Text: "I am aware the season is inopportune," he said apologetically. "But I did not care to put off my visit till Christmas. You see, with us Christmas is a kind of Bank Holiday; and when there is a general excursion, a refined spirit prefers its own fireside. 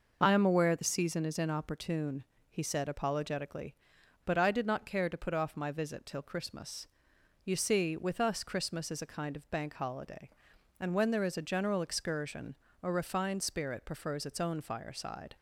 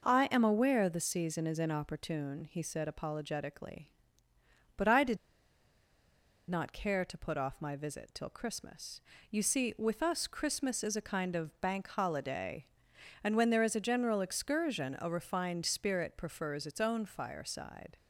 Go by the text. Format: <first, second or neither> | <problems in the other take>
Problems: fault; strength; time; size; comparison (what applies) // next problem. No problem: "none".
first | pauses between "did" and "not"; strong; at 5.1 s; 1.3 s long